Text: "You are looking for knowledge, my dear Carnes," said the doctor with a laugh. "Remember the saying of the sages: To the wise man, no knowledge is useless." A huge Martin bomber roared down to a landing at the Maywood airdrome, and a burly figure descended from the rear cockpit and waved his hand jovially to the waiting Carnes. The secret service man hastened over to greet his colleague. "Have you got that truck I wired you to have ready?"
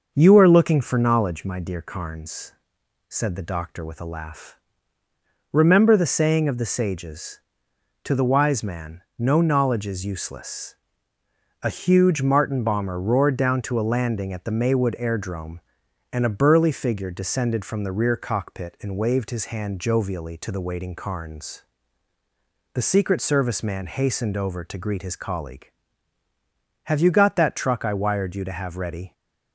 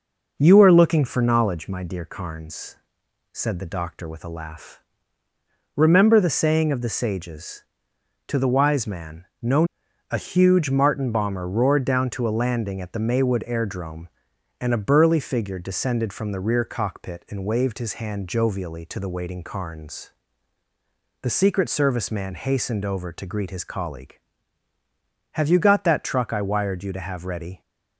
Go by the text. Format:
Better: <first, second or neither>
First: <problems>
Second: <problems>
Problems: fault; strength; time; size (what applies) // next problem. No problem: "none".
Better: first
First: none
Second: skips "knowledge is useless"; at 9.8 s